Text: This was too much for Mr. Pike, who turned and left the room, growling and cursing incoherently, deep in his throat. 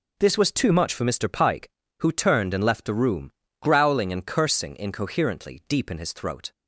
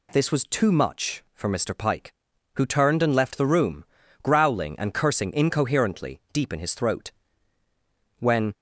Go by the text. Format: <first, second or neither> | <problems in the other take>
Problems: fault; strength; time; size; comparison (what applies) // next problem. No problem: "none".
first | goes on to say "When"; slight; from 8.1 s on; 0.36 s long